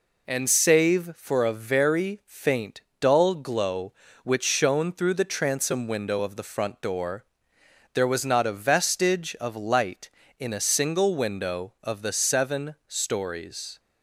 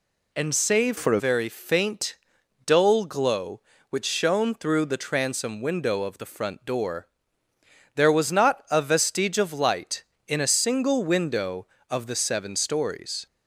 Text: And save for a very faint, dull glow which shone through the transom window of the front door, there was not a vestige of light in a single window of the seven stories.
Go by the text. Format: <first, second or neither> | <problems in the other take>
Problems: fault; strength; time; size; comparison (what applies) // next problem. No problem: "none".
first | changes voice from "for" to "a"; from 0.9 to 1.1 s; 0.2 s long